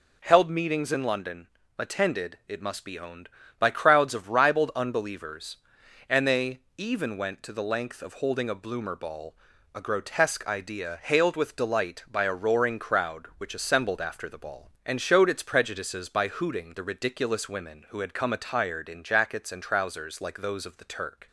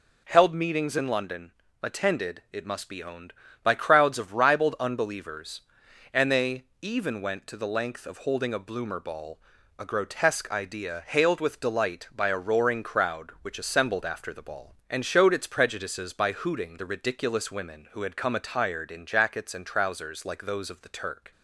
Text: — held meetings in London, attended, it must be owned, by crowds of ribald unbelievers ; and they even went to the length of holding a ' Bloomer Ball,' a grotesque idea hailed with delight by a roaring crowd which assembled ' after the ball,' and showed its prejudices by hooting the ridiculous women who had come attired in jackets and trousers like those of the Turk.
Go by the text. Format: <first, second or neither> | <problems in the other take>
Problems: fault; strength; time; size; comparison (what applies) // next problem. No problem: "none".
neither | pauses between "they" and "even"; slight; the same in both